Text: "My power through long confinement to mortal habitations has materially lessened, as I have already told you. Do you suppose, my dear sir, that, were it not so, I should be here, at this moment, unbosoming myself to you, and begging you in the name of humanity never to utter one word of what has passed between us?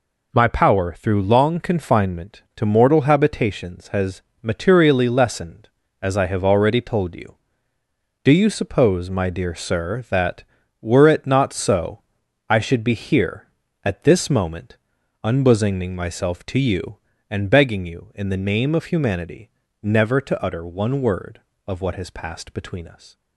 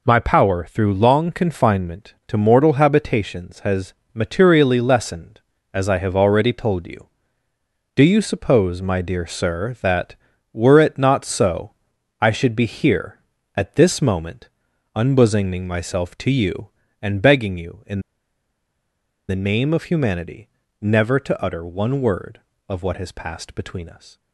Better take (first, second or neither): first